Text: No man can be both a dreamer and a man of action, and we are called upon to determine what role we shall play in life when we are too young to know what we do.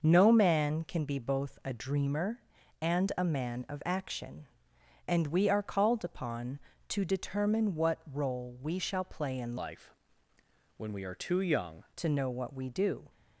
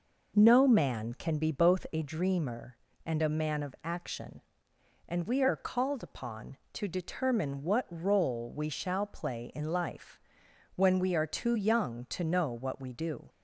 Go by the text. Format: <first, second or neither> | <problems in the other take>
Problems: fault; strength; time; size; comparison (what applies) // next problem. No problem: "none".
second | starts louder than the rest; noticeable; until 1.0 s; 6 dB // changes voice from "life" to "young"; from 9.5 to 11.8 s; 2.3 s long // pauses between "life" and "when"; noticeable; at 9.9 s; 0.82 s long; noticeable in the second